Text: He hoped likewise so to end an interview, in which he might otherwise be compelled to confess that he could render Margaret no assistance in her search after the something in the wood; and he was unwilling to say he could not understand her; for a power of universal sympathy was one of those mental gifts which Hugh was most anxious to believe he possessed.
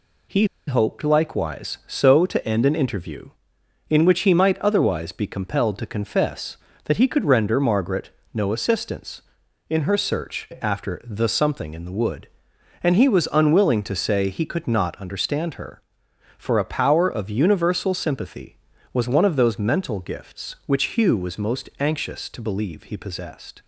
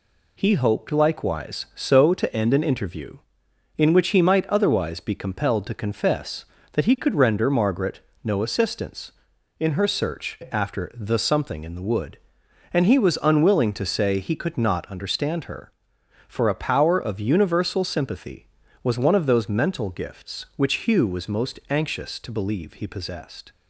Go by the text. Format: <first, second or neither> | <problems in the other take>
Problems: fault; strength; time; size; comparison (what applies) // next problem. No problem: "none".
second | pauses between "He" and "hoped"; slight; at 0.4 s; 0.22 s long // pauses between "Margaret" and "no"; slight; at 8.0 s; 0.24 s long; slight in the second